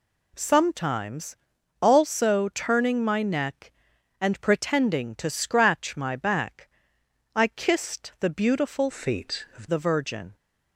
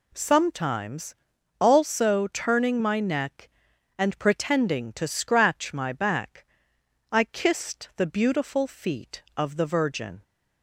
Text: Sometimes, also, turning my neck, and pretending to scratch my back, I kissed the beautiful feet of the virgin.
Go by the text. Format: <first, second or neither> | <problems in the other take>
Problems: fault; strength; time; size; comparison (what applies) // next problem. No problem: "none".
second | changes voice from "feet" to "of"; from 8.9 to 9.6 s; 0.7 s long